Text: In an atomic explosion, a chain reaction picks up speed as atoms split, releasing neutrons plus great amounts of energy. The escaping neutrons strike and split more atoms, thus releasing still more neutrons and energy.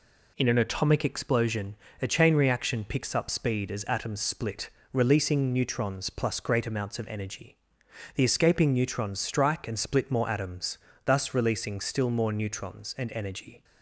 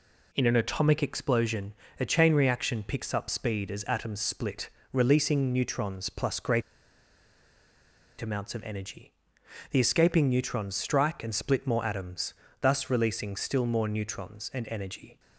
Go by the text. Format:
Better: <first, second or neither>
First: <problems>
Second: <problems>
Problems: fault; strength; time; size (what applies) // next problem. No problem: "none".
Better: first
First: none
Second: pauses between "great" and "amounts"; strong; at 6.6 s; 1.5 s long